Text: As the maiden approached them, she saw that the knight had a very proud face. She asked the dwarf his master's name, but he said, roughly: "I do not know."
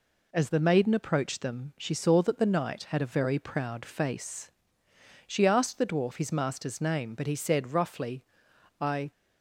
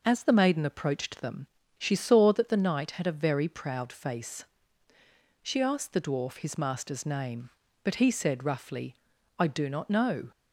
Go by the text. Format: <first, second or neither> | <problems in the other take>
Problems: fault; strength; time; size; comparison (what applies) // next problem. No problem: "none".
second | stops before "do not know"; at 9.1 s